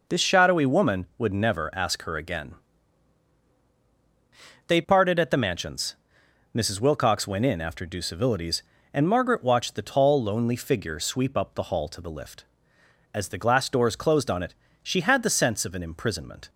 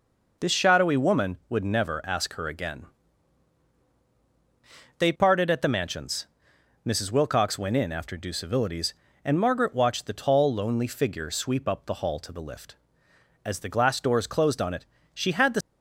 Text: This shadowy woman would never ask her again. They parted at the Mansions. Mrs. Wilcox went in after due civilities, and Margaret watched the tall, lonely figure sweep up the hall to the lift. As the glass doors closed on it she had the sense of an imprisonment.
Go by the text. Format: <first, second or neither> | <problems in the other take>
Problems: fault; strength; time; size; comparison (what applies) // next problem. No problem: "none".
first | pauses between "it" and "she"; slight; at 14.8 s; 0.30 s long; slight in the first // stops before "sense of an imprisonment"; at 15.6 s